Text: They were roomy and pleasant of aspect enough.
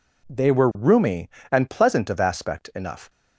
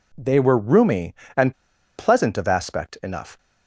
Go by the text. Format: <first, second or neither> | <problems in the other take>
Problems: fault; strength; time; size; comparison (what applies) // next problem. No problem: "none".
first | pauses between "and" and "pleasant"; at 1.5 s; 0.42 s long